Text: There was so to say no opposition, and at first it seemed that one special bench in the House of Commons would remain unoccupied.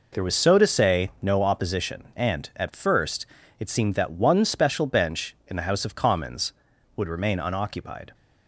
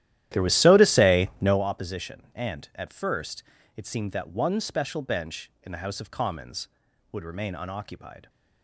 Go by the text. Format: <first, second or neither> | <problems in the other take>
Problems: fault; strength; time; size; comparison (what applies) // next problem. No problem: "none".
first | starts louder than the rest; strong; until 1.6 s; 13 dB // pauses between "first" and "it"; slight; at 3.4 s; 0.34 s long; slight in the first